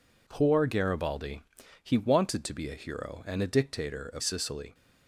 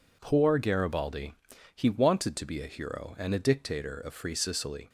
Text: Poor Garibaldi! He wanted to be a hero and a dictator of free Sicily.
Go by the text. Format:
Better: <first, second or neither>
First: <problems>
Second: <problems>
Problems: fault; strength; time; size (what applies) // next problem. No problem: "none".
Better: second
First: skips "free"; at 4.2 s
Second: none